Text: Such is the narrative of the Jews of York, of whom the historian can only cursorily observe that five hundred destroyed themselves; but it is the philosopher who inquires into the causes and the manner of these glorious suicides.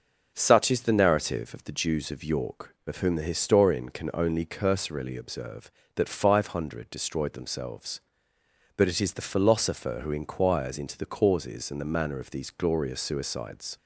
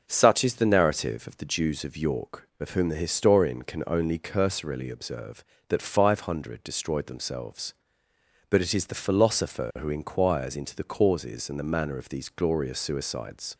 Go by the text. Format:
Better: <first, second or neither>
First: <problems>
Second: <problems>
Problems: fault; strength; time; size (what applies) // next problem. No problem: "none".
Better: neither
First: none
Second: none